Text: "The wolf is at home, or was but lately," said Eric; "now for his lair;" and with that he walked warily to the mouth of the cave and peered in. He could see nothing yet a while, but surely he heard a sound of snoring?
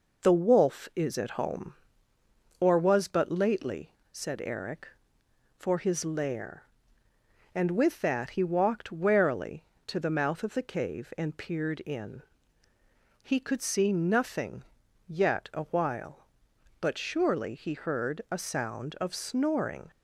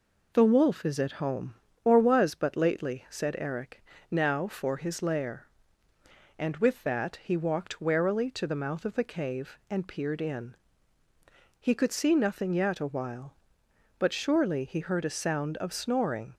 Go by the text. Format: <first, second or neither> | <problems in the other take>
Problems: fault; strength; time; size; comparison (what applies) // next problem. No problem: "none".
second | skips "now"; at 5.2 s // pauses between "nothing" and "yet"; noticeable; at 14.6 s; 0.46 s long